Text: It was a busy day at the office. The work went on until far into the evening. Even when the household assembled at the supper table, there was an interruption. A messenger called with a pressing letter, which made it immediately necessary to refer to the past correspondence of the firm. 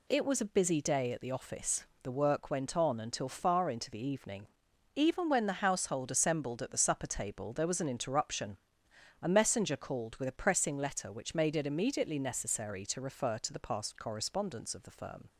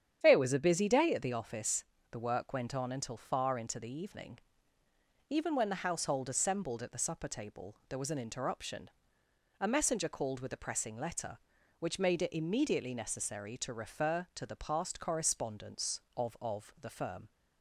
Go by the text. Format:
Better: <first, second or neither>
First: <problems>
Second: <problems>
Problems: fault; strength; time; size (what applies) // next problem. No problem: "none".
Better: first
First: none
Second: starts louder than the rest; strong; until 1.2 s; 9 dB // says "of" twice; at 16.3 s